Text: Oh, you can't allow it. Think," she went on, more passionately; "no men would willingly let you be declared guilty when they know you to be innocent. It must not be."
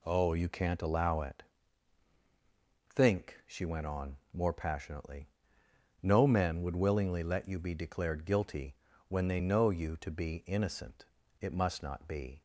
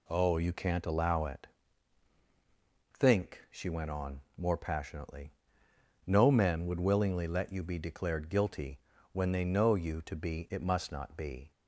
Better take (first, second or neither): first